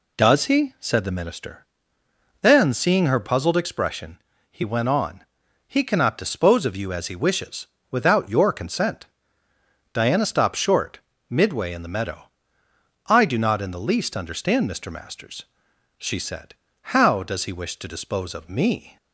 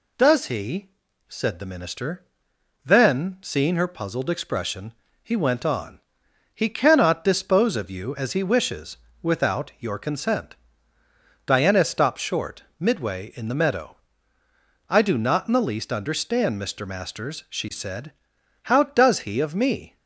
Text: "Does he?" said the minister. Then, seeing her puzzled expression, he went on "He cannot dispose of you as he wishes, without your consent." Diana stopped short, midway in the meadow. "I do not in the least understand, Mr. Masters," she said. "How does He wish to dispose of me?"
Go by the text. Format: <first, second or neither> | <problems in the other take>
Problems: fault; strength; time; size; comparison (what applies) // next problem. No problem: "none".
first | pauses between "on" and "He"; noticeable; at 5.9 s; 0.54 s long; also in the first // skips "wish to dispose"; at 19.3 s